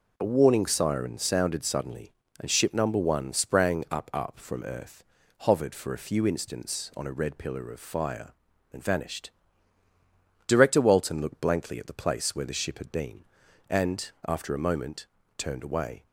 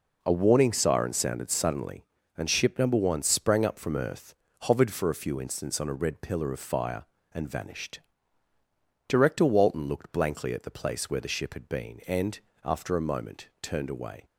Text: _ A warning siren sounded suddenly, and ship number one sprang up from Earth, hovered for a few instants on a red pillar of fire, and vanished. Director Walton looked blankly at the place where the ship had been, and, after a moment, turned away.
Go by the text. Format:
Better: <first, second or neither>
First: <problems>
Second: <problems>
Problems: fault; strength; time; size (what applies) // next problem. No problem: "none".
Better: second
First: says "up" twice; at 4.1 s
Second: none